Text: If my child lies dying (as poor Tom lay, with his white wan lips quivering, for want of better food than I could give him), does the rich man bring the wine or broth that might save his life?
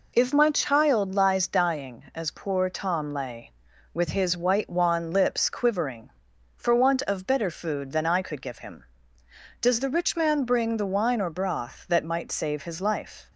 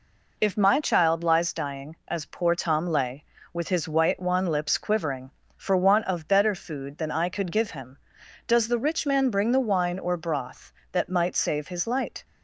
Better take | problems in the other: first | says "light" for "life"; at 11.8 s

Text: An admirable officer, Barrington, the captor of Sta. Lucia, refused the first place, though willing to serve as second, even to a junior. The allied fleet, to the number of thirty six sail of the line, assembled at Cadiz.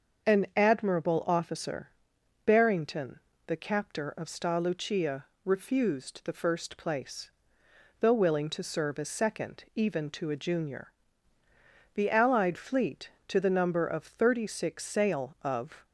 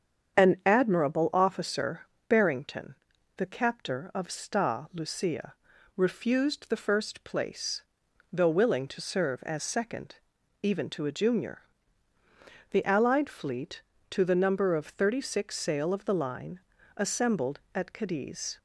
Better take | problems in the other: second | starts louder than the rest; until 1.3 s; 6.5 dB; strong in the second // stops before "the line assembled at Cadiz"; at 15.8 s

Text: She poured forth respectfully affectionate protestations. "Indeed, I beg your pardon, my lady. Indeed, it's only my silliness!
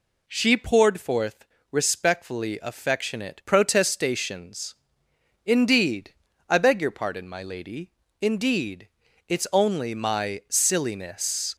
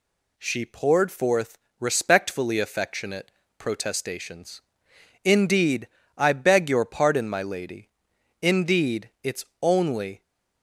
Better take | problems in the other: first | pauses between "forth" and "respectfully"; slight; at 1.5 s; 0.22 s long; slight in the first // pauses between "affectionate" and "protestations"; slight; at 3.3 s; 0.26 s long // pauses between "it's" and "only"; slight; at 9.4 s; 0.18 s long // stops before "my silliness"; at 10.2 s

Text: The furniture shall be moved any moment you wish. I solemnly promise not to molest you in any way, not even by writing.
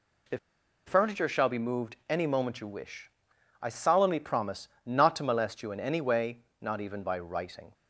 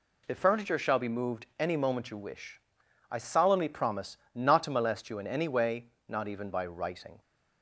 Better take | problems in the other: second | pauses between "The" and "furniture"; noticeable; at 0.3 s; 0.47 s long // pauses between "promise" and "not"; slight; at 4.6 s; 0.18 s long; slight in the second

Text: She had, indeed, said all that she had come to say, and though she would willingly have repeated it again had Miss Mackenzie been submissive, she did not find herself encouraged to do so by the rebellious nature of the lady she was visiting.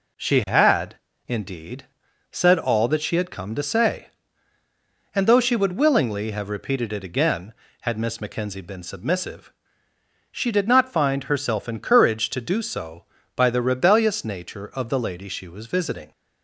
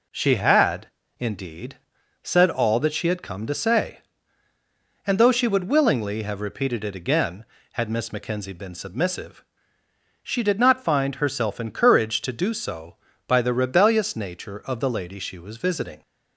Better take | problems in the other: neither | none

